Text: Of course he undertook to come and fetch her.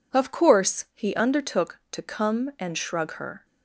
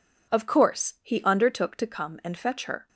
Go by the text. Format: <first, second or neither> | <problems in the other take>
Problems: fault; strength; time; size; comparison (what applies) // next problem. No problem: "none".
second | says "shrug" for "fetch"; at 2.7 s